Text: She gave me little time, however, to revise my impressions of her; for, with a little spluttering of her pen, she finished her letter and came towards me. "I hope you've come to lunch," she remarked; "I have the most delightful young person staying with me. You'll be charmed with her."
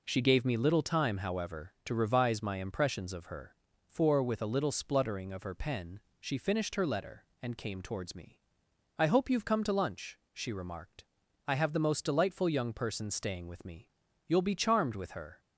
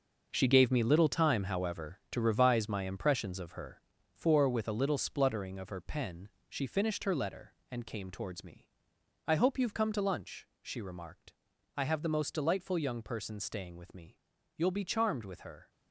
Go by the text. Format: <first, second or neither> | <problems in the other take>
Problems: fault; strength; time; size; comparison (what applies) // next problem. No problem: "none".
first | gets quieter; strong; throughout; 10.5 dB